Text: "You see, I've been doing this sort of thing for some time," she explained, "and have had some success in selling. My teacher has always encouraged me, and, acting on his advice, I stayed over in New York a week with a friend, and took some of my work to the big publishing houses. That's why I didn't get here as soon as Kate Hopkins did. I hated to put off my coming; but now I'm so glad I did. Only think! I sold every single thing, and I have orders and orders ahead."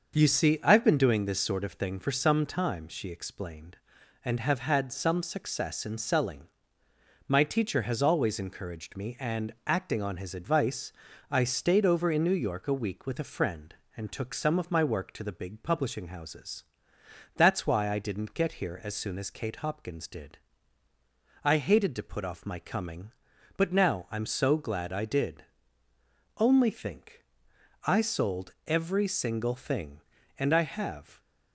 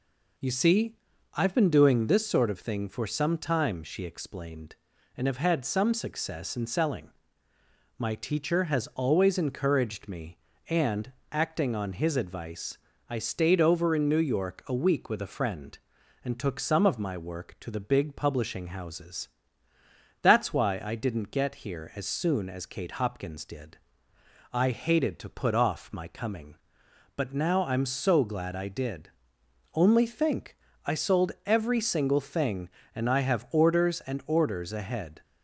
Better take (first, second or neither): second